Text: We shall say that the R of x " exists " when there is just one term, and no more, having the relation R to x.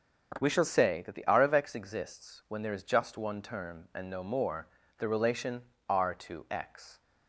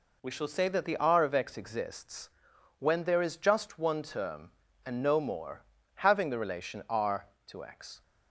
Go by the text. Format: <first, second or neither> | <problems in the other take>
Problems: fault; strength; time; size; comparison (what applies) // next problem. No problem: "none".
second | starts louder than the rest; until 1.4 s; 7 dB // skips "having"; at 4.8 s // pauses between "relation" and "R"; slight; at 5.6 s; 0.20 s long